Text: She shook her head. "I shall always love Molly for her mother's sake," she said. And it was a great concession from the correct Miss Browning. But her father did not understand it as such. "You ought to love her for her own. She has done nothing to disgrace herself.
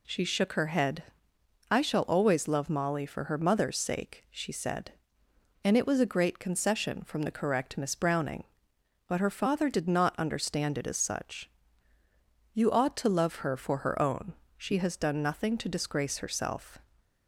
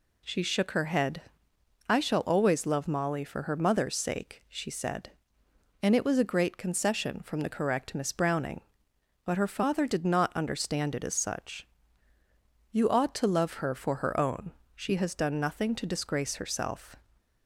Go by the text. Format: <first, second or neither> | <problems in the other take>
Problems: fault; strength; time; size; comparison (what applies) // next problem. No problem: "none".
neither | none